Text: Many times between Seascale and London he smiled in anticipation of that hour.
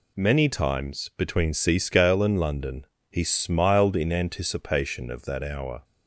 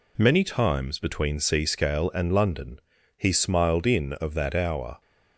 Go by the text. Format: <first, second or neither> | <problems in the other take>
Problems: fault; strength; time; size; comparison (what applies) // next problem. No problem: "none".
first | pauses between "London" and "he"; at 2.8 s; 0.38 s long; slight in the first // skips "anticipation"; at 4.1 s